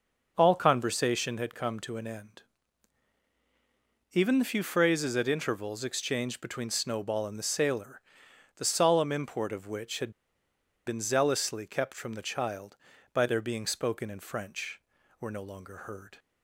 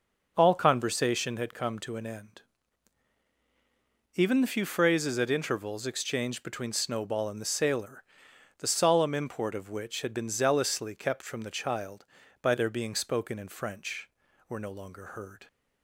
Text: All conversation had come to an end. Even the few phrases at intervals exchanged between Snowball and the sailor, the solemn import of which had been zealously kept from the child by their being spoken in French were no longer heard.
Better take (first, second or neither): second